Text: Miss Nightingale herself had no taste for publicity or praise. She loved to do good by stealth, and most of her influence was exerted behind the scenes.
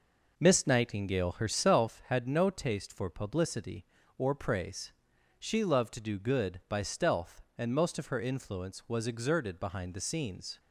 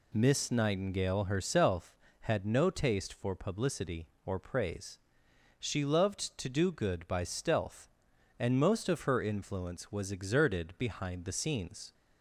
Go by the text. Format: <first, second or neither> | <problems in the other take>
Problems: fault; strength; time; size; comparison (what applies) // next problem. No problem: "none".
second | starts louder than the rest; noticeable; until 1.9 s; 5 dB